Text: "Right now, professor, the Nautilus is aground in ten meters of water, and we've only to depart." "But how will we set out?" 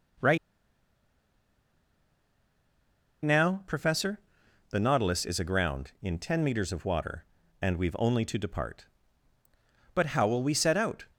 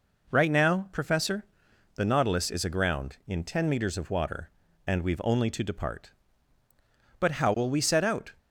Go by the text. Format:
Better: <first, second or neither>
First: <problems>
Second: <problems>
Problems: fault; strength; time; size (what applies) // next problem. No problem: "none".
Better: second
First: pauses between "Right" and "now"; strong; at 0.3 s; 2.8 s long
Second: none